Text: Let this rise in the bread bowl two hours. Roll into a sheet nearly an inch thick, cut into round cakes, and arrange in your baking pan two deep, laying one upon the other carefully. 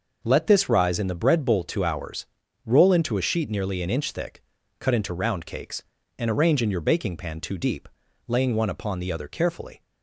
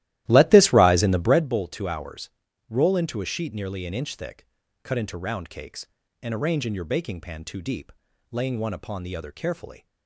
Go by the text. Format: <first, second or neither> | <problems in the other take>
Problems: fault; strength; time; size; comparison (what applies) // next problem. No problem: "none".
first | starts louder than the rest; strong; until 1.5 s; 14.5 dB